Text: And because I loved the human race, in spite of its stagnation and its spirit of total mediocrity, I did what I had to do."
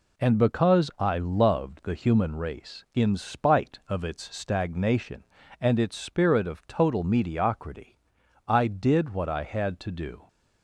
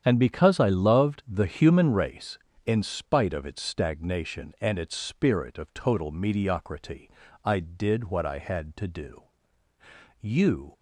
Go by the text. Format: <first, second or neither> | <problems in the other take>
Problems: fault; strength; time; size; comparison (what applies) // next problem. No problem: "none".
first | starts louder than the rest; strong; until 1.0 s; 9 dB // goes on to say "You"; from 10.1 s on; 0.54 s long